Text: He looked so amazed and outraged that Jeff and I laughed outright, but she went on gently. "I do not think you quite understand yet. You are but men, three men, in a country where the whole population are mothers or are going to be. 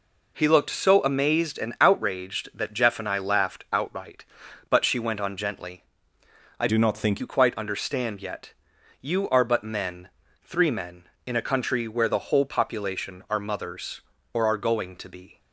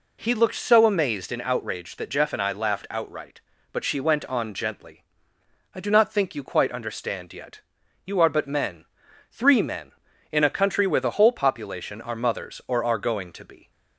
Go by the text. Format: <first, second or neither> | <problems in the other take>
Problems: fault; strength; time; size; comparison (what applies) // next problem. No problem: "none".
second | changes voice from "do" to "think"; from 6.6 to 7.2 s; 0.6 s long